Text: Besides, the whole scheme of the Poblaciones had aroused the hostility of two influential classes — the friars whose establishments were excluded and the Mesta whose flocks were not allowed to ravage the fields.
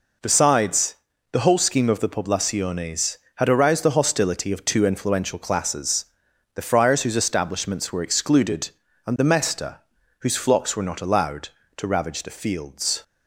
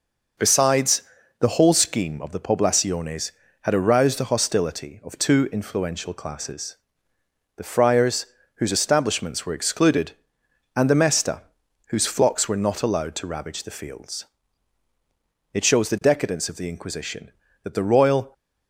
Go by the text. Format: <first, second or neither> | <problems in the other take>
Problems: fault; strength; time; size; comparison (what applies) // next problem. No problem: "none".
first | pauses between "friars" and "whose"; slight; at 8.2 s; 0.30 s long // pauses between "Mesta" and "whose"; noticeable; at 11.4 s; 0.46 s long; also in the first // goes on to say "It shows the decadence of the Inquisition that the royal"; strong; from 15.5 s on; 2.8 s long